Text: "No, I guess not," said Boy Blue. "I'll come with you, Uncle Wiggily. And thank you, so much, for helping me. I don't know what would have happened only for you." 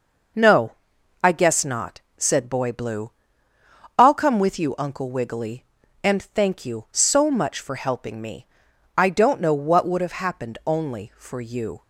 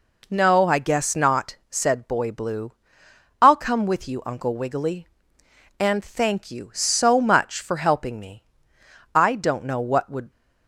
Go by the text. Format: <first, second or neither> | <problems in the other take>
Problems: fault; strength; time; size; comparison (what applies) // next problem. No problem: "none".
first | stops before "have happened only for you"; at 10.2 s